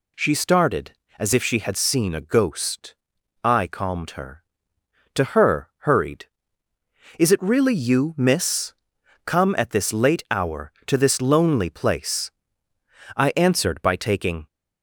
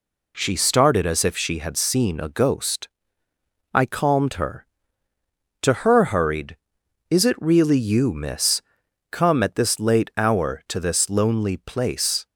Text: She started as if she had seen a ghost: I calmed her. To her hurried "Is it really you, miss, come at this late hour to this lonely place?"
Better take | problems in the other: second | goes on to say "I answered by taking"; noticeable; from 13.1 s on; 1.3 s long

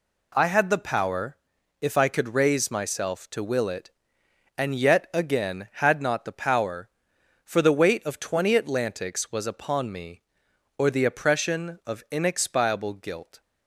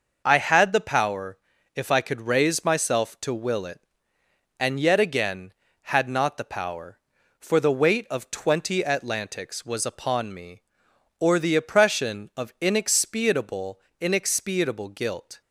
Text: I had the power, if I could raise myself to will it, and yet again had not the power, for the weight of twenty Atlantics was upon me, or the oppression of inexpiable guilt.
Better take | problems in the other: first | says "inexpiable" twice; at 13.9 s

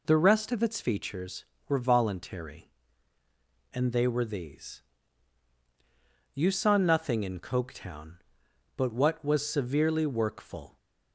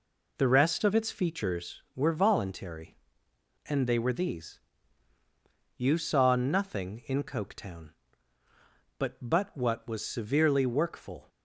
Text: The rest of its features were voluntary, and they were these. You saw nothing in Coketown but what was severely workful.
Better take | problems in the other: first | says "but" twice; at 9.2 s

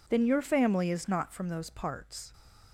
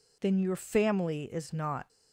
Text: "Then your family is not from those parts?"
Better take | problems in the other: first | stops before "from those parts"; at 1.8 s

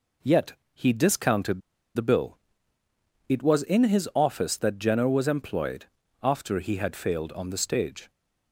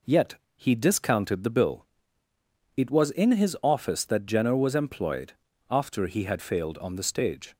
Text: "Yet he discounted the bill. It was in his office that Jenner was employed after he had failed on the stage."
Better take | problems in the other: second | pauses between "Yet" and "he"; slight; at 0.5 s; 0.20 s long; slight in the second // pauses between "discounted" and "the"; slight; at 1.6 s; 0.34 s long // pauses between "employed" and "after"; slight; at 5.8 s; 0.36 s long; slight in the second

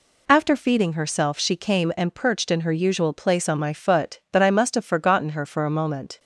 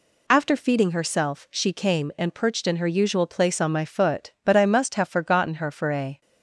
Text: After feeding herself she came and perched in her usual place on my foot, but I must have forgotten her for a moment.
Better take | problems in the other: first | stops before "moment"; at 6.2 s

